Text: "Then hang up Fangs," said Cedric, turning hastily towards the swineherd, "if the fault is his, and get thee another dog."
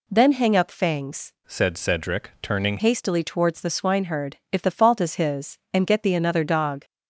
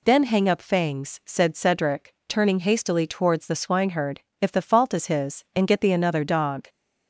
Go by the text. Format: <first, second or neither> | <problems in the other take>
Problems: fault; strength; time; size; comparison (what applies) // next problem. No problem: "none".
second | changes voice from "said" to "turning"; from 1.4 to 2.7 s; 1.3 s long